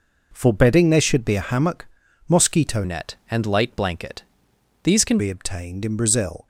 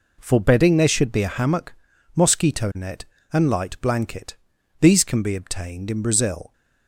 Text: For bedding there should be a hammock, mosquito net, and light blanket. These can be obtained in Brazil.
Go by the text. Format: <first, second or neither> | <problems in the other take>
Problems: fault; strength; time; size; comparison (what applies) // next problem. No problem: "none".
second | changes voice from "net" to "can"; from 2.8 to 5.1 s; 2.3 s long